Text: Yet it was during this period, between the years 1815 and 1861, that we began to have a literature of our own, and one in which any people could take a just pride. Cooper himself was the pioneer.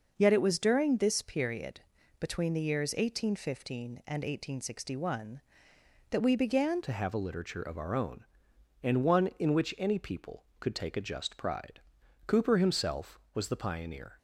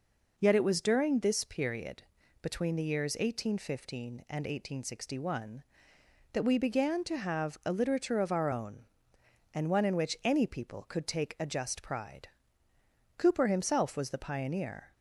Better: second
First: changes voice at "to"; from 6.8 s on; 7.3 s long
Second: none

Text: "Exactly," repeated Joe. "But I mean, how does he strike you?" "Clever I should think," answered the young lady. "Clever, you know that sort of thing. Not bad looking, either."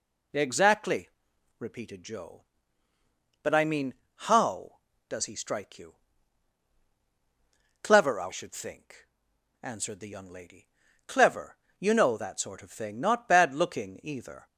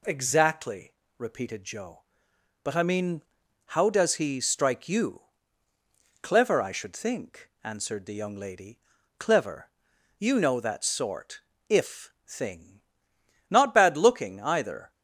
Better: first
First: none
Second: says "if" for "of"; at 11.6 s

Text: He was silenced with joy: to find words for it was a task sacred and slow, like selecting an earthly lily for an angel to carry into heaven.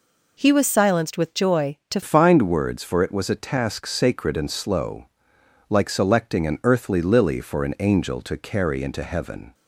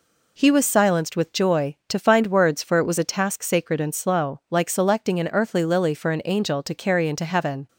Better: second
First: changes voice at "find"; from 2.0 s on; 7.5 s long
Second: none

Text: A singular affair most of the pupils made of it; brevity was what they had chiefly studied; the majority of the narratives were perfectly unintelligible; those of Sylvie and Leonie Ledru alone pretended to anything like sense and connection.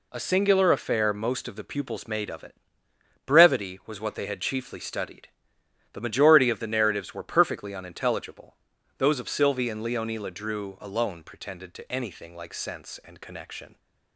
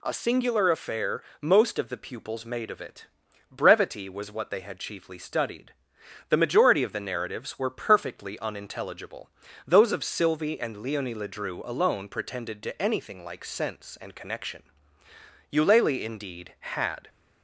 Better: first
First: none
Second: pauses between "affair" and "most"; slight; at 1.2 s; 0.20 s long // goes on to say "Eulalie indeed had"; from 15.4 s on; 1.5 s long

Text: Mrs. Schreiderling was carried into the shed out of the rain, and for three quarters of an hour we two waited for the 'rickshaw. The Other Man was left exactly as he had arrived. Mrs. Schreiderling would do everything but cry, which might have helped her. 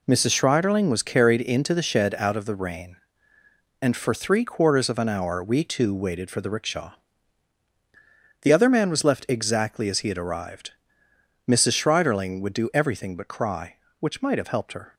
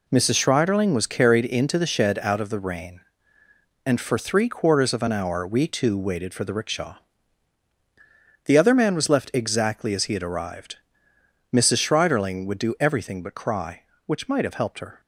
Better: neither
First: none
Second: none

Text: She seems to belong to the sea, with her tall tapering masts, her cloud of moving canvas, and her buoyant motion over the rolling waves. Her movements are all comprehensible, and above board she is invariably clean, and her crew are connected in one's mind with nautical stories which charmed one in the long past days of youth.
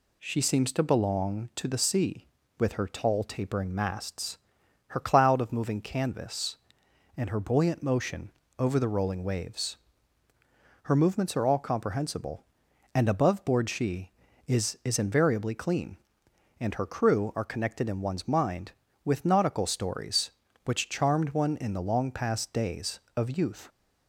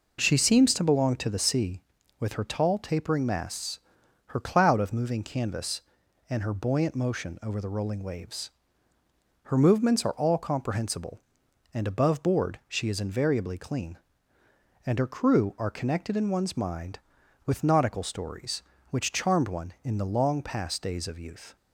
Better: second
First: pauses between "motion" and "over"; slight; at 8.2 s; 0.30 s long // says "is" twice; at 14.8 s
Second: none

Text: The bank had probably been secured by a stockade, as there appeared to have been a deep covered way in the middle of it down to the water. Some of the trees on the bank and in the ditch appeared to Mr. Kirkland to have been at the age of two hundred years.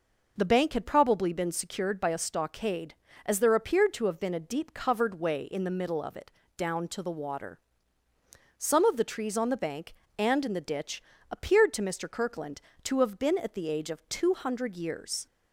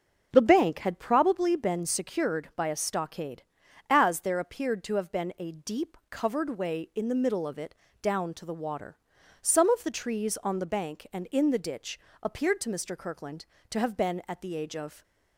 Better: first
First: pauses between "it" and "down"; slight; at 6.2 s; 0.28 s long // pauses between "ditch" and "appeared"; slight; at 11.0 s; 0.28 s long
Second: starts louder than the rest; until 1.3 s; 6.5 dB // pauses between "it" and "down"; slight; at 7.7 s; 0.26 s long // pauses between "ditch" and "appeared"; slight; at 11.9 s; 0.22 s long // stops before "two hundred years"; at 15.0 s

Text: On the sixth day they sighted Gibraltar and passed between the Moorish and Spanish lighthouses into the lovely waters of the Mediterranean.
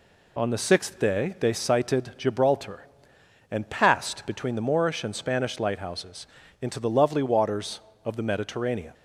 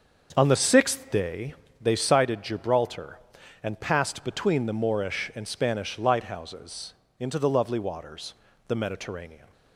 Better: first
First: pauses between "lighthouses" and "into"; slight; at 6.2 s; 0.34 s long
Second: starts louder than the rest; until 1.3 s; 6.5 dB // pauses between "day" and "they"; slight; at 1.5 s; 0.26 s long // pauses between "lighthouses" and "into"; slight; at 6.9 s; 0.26 s long // skips "of"; at 8.5 s

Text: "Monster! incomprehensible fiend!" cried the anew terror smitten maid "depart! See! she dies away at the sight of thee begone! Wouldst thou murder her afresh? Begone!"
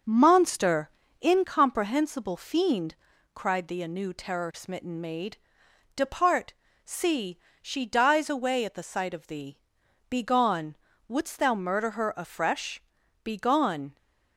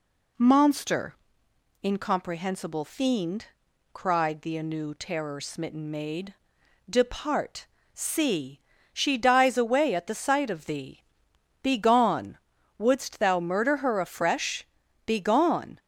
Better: second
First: starts louder than the rest; noticeable; until 1.4 s; 6 dB // pauses between "maid" and "depart"; noticeable; at 5.3 s; 0.60 s long // pauses between "thee" and "begone"; noticeable; at 9.5 s; 0.50 s long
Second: pauses between "maid" and "depart"; noticeable; at 6.3 s; 0.56 s long // pauses between "thee" and "begone"; noticeable; at 11.0 s; 0.57 s long

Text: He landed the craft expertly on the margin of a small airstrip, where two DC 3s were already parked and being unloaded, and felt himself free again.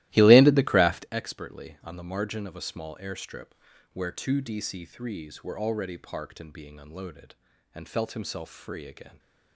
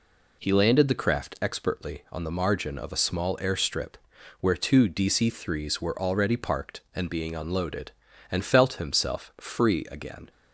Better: second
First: starts louder than the rest; strong; until 1.1 s; 16.5 dB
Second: none

